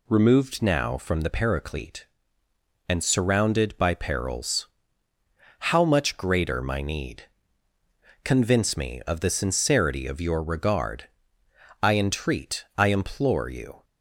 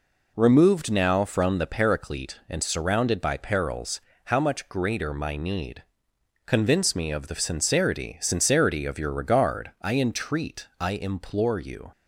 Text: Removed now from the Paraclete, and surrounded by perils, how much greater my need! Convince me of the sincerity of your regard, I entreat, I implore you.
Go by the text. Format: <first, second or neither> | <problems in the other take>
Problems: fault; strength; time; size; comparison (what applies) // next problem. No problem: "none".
first | says "sincerity" twice; at 8.1 s